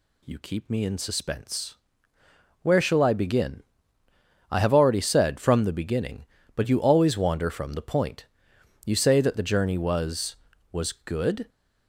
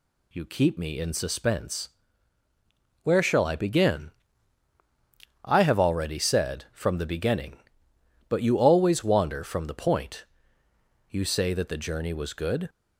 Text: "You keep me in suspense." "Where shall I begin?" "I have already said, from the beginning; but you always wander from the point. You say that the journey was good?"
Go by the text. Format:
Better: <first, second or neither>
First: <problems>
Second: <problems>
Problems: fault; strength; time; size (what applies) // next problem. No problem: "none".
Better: second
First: says "was" twice; at 10.7 s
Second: none